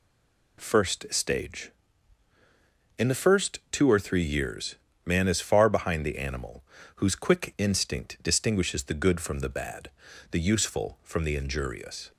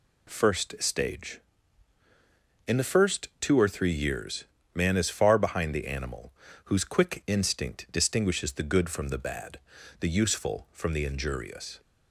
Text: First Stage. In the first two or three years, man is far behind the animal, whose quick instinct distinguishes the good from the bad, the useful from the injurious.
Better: second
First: stays silent before the first word; slight; until 0.5 s; 0.5 s long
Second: none

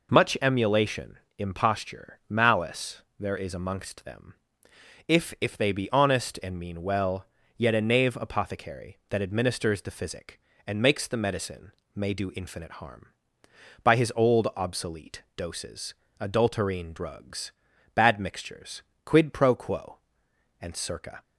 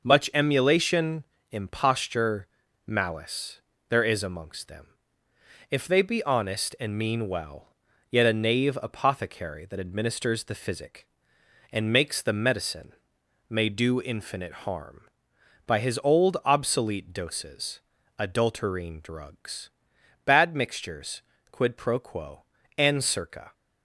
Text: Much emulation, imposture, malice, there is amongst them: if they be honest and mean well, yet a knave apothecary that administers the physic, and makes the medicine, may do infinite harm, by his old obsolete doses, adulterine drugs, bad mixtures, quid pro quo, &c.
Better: second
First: says "if" twice; at 5.4 s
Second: none

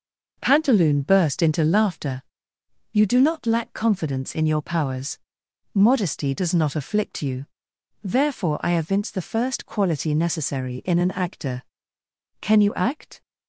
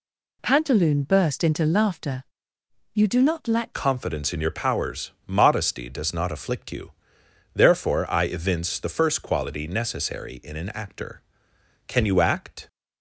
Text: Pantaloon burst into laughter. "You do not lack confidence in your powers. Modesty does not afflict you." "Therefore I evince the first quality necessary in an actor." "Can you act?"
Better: first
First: none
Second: changes voice at "confidence"; from 3.7 s on; 8.9 s long

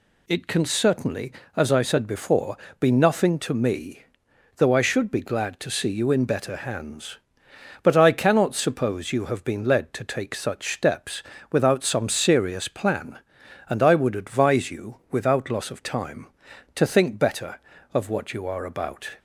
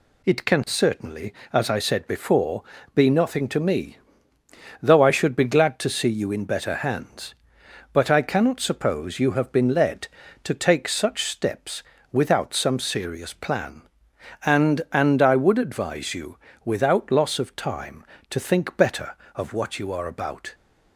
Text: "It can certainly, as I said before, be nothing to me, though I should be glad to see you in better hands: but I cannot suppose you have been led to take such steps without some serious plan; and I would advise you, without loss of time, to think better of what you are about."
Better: first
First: pauses between "steps" and "without"; slight; at 11.2 s; 0.30 s long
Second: pauses between "steps" and "without"; slight; at 11.8 s; 0.30 s long // says "and" twice; at 14.9 s

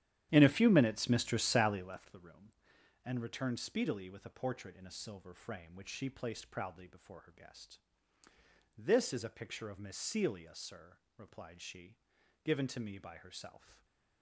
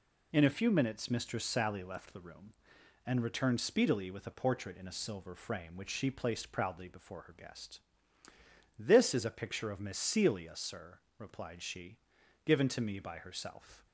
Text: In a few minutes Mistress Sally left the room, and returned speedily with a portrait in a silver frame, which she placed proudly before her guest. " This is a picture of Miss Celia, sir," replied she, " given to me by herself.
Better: second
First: starts louder than the rest; strong; until 2.0 s; 11.5 dB // stays silent after the last word; slight; from 13.5 s on; 0.7 s long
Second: none

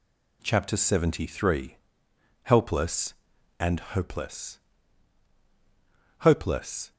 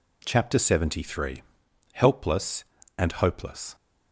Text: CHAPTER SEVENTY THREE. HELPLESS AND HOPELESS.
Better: second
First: says "HOPELESS" twice; at 6.1 s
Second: none

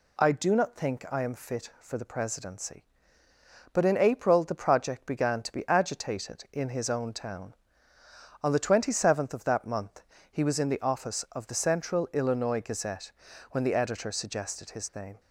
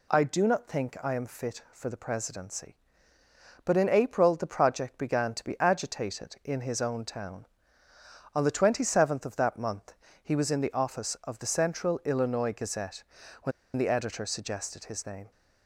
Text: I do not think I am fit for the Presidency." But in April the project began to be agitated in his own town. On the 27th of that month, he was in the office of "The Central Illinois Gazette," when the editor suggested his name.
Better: first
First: none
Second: pauses between "when" and "the"; slight; at 13.5 s; 0.25 s long

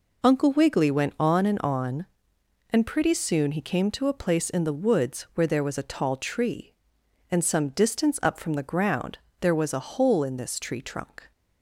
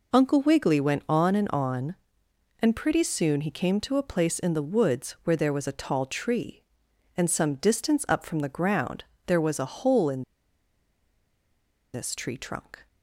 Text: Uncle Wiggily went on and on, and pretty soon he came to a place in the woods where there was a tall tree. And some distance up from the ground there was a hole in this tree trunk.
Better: first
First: pauses between "ground" and "there"; slight; at 9.1 s; 0.22 s long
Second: pauses between "ground" and "there"; slight; at 9.0 s; 0.22 s long // pauses between "in" and "this"; strong; at 10.2 s; 1.7 s long

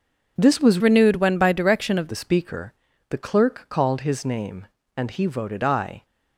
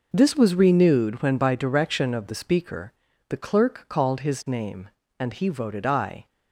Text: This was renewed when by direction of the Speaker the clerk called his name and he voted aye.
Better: second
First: changes voice from "renewed" to "of"; from 0.8 to 2.0 s; 1.2 s long // pauses between "Speaker" and "the"; at 2.7 s; 0.38 s long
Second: pauses between "Speaker" and "the"; at 2.9 s; 0.38 s long

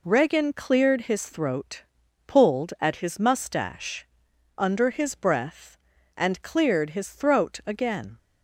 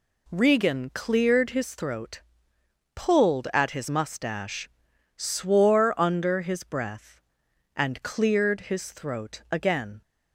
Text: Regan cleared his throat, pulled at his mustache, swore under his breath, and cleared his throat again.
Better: second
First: skips "swore"; at 4.3 s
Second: none

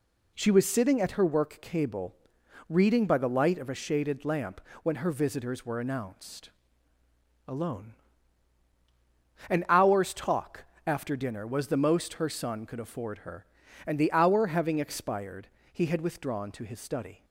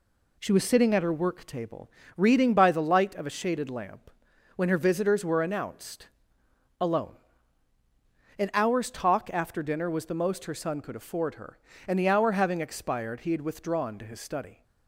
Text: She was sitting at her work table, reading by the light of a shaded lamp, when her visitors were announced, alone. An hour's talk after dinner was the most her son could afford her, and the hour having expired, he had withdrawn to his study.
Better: second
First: says "cable" for "table"; at 1.6 s // pauses between "talk" and "after"; slight; at 10.6 s; 0.22 s long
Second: none

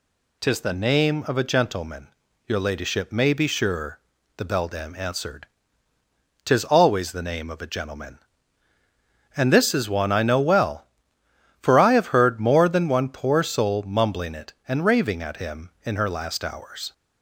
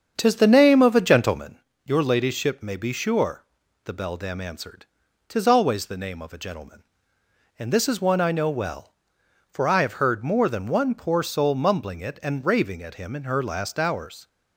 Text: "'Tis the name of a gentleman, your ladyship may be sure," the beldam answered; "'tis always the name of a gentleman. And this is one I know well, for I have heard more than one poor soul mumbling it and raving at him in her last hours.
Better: first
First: none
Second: starts louder than the rest; strong; until 1.5 s; 7.5 dB

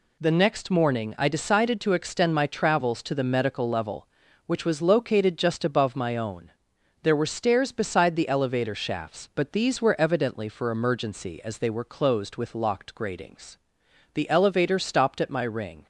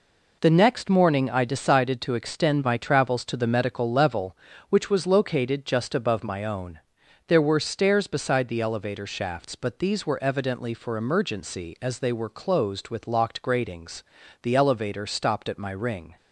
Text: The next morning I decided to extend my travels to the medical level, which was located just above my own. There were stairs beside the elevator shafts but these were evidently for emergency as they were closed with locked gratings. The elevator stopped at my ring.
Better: neither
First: none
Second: none

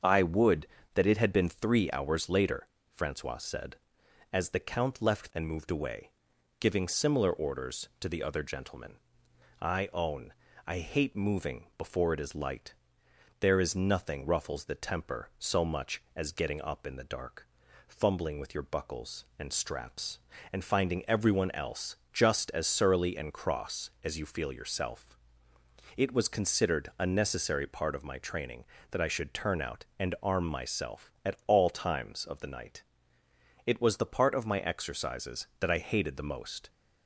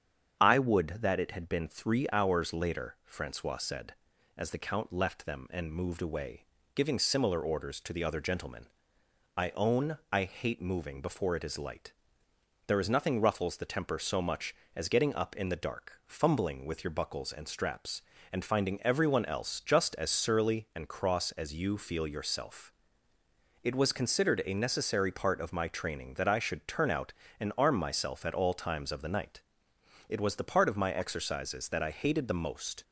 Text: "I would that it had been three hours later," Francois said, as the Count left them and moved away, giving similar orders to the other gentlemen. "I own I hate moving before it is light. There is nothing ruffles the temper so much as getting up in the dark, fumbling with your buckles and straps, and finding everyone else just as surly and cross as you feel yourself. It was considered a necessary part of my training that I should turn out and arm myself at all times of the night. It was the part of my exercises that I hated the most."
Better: second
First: starts louder than the rest; until 1.3 s; 7 dB // skips "them"; at 5.3 s // pauses between "own" and "I"; slight; at 10.3 s; 0.34 s long // pauses between "else" and "just"; slight; at 21.9 s; 0.18 s long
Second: starts louder than the rest; strong; until 1.4 s; 8 dB

